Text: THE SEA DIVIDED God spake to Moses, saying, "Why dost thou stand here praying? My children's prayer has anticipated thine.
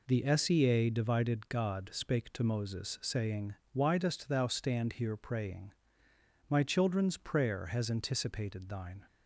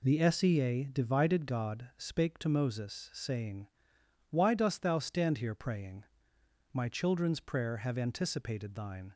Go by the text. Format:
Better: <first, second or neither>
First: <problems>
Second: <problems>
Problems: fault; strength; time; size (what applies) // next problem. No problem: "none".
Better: first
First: none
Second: says "have" for "has"; at 7.7 s